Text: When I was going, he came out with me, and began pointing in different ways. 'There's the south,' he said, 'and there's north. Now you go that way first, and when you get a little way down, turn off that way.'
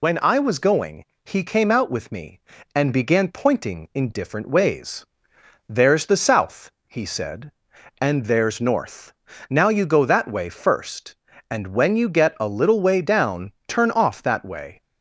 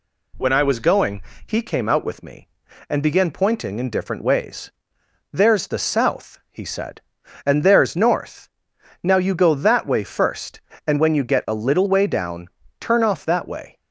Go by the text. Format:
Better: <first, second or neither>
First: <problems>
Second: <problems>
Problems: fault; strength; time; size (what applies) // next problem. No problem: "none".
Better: second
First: loses the start of "When"; at 0.0 s; 65 ms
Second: none